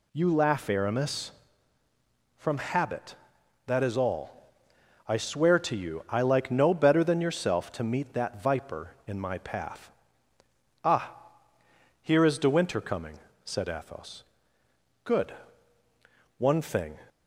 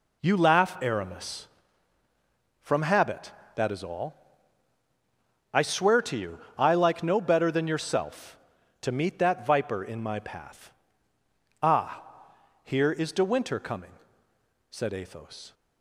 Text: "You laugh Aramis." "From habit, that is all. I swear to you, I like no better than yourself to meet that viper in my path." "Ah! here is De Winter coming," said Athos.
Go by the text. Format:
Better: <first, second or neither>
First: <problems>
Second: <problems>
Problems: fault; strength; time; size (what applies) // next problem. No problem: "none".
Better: second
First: goes on to say "Good one thing"; strong; from 15.0 s on; 1.9 s long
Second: none